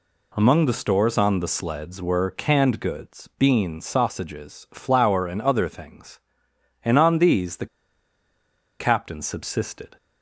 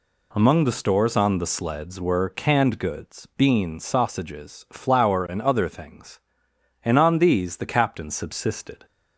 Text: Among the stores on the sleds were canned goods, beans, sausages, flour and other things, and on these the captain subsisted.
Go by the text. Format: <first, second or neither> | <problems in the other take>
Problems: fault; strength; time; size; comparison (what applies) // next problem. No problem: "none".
second | pauses between "the" and "captain"; at 7.6 s; 1.1 s long